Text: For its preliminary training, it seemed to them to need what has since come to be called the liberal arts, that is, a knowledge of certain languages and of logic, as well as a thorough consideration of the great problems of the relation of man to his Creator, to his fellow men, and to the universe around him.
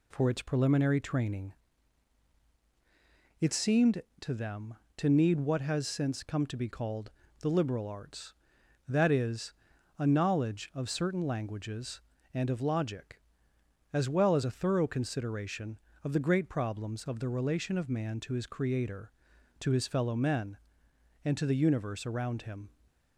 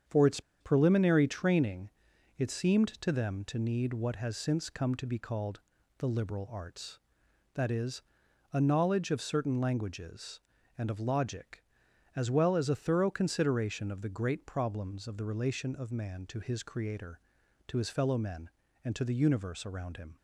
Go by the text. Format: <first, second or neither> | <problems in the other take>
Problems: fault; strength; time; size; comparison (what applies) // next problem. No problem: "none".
first | starts louder than the rest; strong; until 1.2 s; 7.5 dB // pauses between "its" and "preliminary"; slight; at 0.3 s; 0.20 s long // pauses between "called" and "the"; at 5.5 s; 0.38 s long; slight in the first